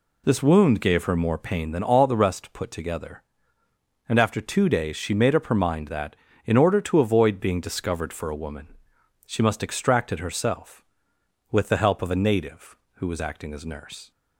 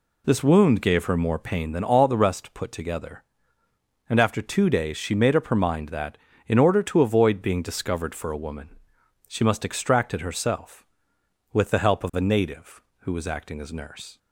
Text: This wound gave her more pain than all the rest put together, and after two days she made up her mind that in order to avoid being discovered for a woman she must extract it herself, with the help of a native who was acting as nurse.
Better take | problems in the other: neither | pauses between "woman" and "she"; noticeable; the same in both

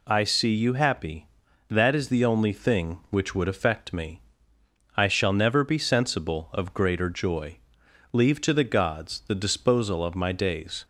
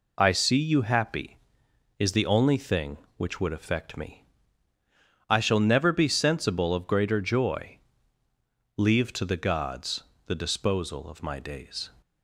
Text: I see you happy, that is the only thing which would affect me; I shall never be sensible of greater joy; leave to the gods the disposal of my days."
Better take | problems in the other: first | skips "that"; at 1.6 s // pauses between "gods" and "the"; slight; at 10.0 s; 0.22 s long

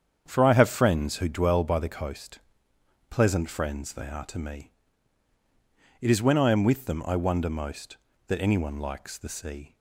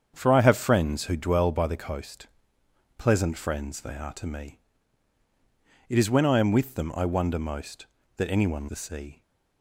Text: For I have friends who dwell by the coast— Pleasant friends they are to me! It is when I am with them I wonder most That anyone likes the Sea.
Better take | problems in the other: first | starts louder than the rest; strong; until 1.1 s; 7.5 dB; strong in the first // skips "likes"; at 8.6 s

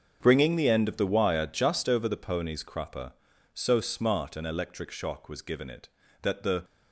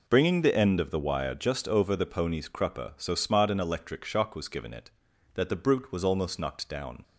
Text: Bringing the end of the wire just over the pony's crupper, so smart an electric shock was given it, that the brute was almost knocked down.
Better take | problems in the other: second | starts louder than the rest; until 1.2 s; 7 dB // stops before "brute was almost knocked down"; at 6.6 s

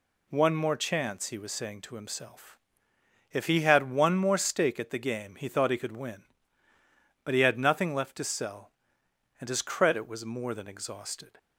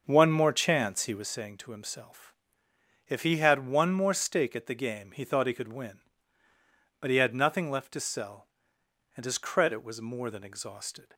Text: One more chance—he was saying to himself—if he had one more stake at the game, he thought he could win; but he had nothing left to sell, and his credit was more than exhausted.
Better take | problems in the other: first | starts louder than the rest; until 1.3 s; 6.5 dB

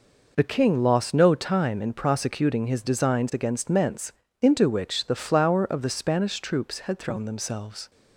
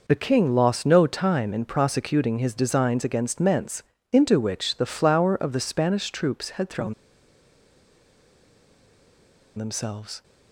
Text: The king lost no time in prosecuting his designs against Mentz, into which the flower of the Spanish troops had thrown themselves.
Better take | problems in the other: first | pauses between "thrown" and "themselves"; strong; at 6.9 s; 2.6 s long

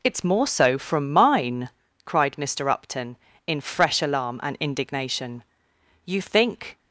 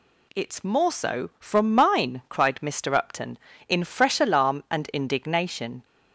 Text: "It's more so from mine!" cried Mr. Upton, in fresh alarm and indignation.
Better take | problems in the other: second | goes on to say "You think"; noticeable; from 6.0 s on; 0.72 s long

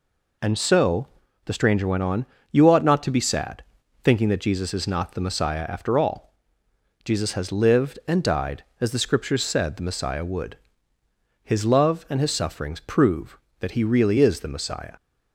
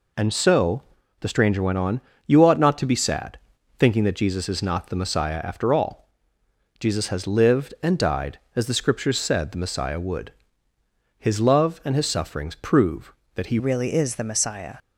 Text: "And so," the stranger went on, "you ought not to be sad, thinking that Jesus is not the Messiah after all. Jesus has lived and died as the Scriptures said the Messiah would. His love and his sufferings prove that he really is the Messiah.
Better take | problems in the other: first | changes voice at "really"; from 13.5 s on; 1.2 s long

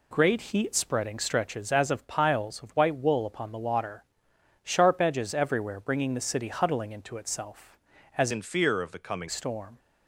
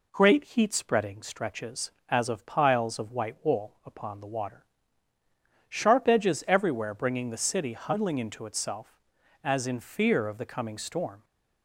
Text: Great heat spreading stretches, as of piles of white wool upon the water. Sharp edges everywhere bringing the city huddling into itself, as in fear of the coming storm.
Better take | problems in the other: second | changes voice from "in" to "coming"; from 8.3 to 9.2 s; 0.9 s long

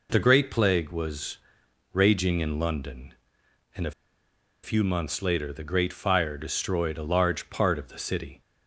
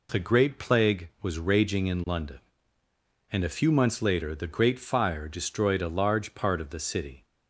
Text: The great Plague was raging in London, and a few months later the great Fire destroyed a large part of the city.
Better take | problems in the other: second | pauses between "was" and "raging"; noticeable; at 1.3 s; 0.56 s long // pauses between "a" and "few"; noticeable; at 3.9 s; 0.70 s long

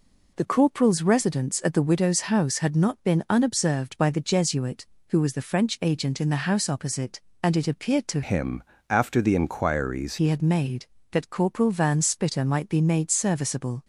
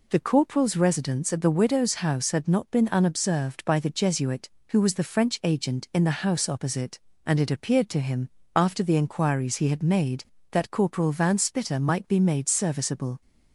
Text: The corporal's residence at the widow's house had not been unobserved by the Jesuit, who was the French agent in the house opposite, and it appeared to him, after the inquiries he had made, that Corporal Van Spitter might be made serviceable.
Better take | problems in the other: second | changes voice from "him" to "inquiries"; from 8.2 to 10.1 s; 1.9 s long

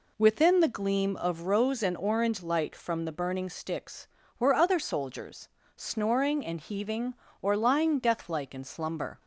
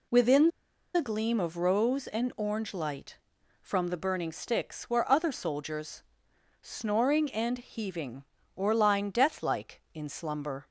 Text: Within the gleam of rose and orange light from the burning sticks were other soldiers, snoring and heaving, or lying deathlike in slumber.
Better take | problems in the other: first | pauses between "Within" and "the"; noticeable; at 0.4 s; 0.46 s long

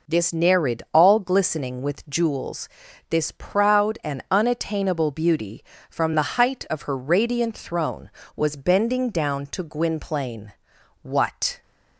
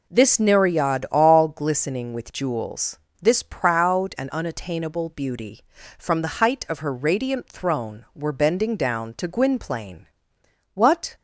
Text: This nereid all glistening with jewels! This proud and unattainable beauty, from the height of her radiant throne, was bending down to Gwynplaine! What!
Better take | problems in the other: first | says "were" for "was"; at 8.1 s

